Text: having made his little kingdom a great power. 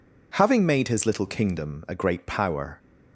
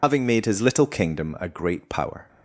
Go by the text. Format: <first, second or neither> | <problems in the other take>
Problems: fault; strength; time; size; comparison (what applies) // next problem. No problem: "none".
first | loses the start of "having"; at 0.0 s; 60 ms